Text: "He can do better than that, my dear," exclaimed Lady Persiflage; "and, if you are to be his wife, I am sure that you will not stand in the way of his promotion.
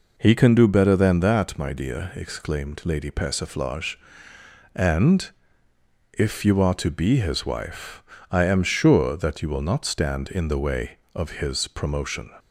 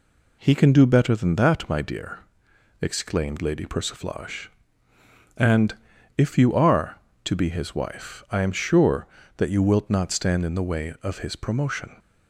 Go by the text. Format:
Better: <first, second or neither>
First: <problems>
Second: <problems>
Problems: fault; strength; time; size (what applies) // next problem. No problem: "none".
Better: first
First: none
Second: says "wilt" for "will"; at 9.6 s